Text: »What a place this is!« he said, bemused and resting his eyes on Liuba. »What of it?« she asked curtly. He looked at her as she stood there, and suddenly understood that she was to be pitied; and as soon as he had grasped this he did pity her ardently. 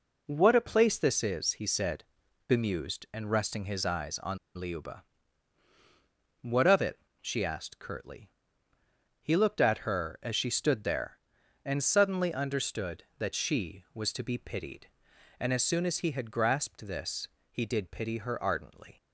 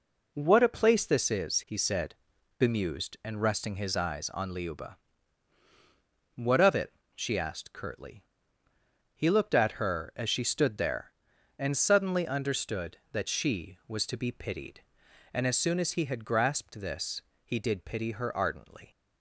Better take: second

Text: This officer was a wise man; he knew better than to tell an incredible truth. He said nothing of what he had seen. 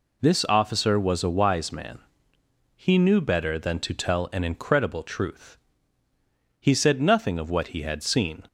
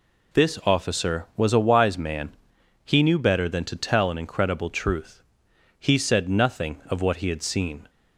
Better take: neither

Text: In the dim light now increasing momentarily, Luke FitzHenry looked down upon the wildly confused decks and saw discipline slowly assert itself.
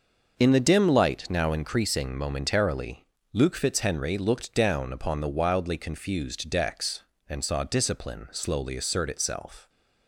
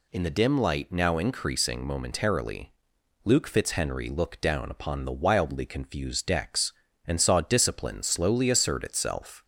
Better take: neither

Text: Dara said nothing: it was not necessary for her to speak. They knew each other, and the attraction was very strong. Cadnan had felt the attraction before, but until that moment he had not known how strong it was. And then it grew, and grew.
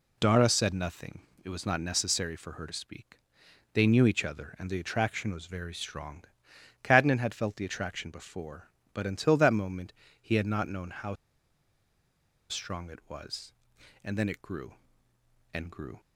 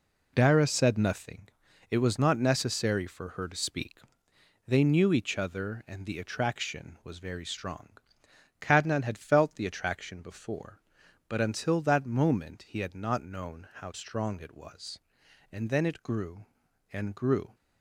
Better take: second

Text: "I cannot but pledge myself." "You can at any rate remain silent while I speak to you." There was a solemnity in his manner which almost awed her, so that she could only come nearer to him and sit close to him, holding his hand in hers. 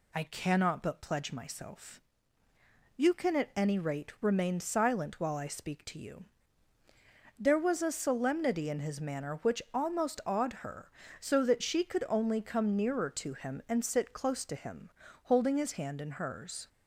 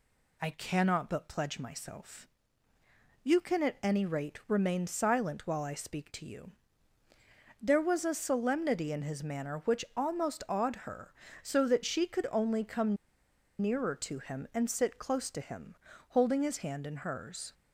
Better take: first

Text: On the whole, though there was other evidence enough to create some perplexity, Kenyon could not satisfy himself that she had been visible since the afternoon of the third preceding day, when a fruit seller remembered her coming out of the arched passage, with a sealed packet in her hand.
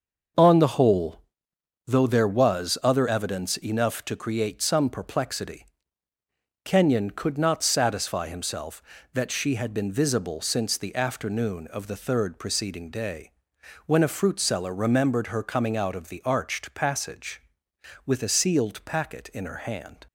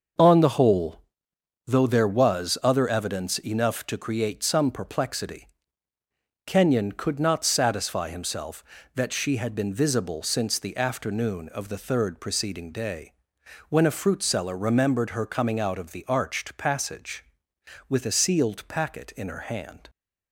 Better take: neither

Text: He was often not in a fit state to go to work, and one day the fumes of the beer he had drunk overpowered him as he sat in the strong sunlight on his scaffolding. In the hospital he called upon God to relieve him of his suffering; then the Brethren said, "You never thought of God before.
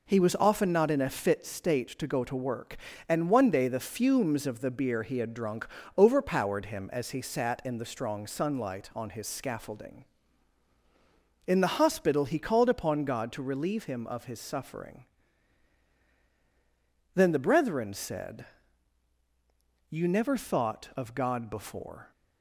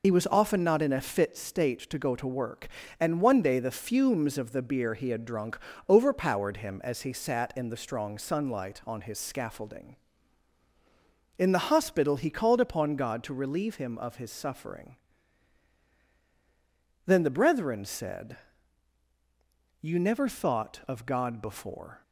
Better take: first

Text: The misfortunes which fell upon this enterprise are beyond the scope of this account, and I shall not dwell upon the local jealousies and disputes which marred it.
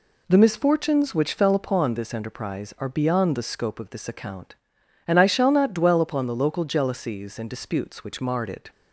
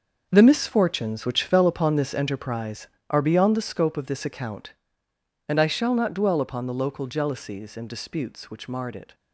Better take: first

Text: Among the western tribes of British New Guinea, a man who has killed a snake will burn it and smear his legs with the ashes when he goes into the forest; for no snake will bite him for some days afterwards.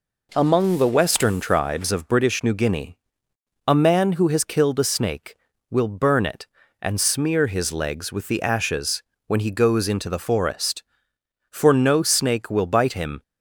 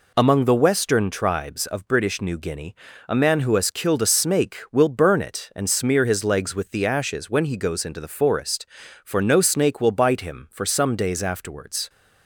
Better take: second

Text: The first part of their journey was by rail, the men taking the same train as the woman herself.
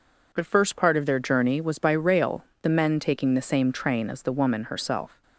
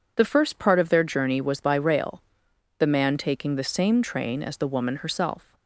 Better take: first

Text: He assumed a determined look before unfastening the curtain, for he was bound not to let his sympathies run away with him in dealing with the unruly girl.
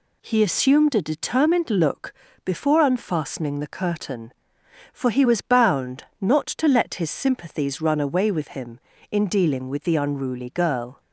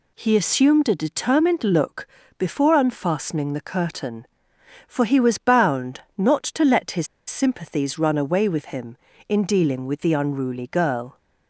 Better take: first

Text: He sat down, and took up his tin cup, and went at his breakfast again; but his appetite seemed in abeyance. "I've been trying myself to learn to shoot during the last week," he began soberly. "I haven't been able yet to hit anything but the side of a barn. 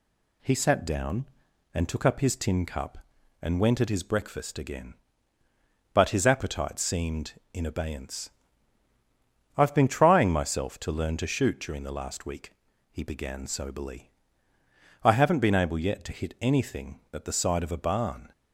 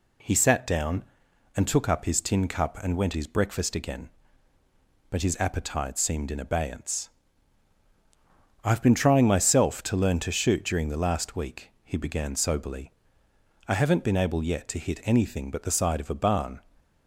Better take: first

